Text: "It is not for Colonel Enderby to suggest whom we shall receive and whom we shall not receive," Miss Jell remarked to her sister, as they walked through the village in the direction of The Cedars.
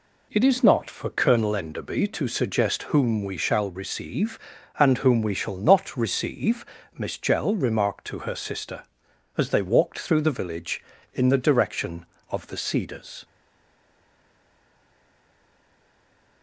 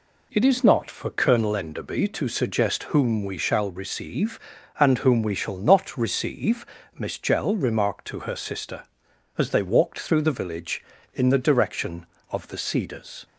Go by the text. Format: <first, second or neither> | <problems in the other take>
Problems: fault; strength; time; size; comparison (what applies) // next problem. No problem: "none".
second | stays silent after the last word; strong; from 13.2 s on; 3.2 s long